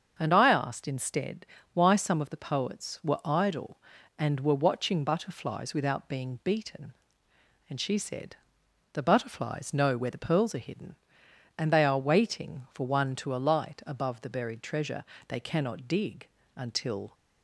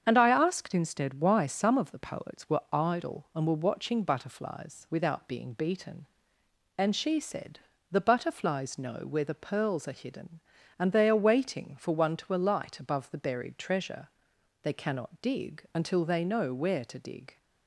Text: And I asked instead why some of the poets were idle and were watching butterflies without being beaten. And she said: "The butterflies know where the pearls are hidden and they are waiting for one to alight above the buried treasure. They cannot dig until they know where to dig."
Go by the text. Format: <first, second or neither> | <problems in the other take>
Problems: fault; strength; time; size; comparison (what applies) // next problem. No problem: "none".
second | starts louder than the rest; until 1.2 s; 7 dB; strong in the second // pauses between "instead" and "why"; slight; at 1.4 s; 0.28 s long // pauses between "dig" and "until"; slight; at 16.2 s; 0.28 s long // stops before "they know where to dig"; at 17.1 s